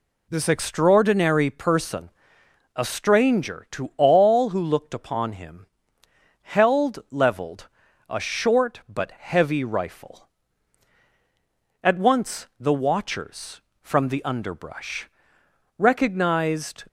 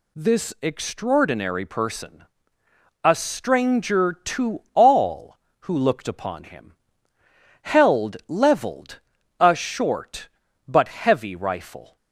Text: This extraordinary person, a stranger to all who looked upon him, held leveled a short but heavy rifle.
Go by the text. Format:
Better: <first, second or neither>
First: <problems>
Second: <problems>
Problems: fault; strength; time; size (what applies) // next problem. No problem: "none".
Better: second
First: pauses between "leveled" and "a"; at 7.6 s; 0.42 s long // goes on to say "At once the watchers from the underbrush recognized"; strong; from 11.8 s on; 5.0 s long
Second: pauses between "leveled" and "a"; at 8.9 s; 0.40 s long